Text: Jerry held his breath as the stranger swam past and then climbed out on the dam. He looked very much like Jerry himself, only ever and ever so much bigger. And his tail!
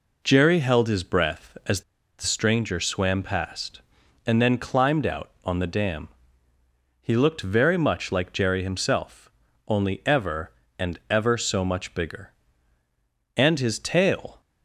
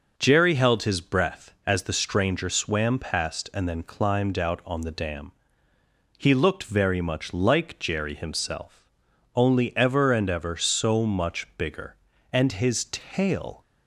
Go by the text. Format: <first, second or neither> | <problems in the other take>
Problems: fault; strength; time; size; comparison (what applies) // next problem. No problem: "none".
second | pauses between "as" and "the"; at 1.8 s; 0.37 s long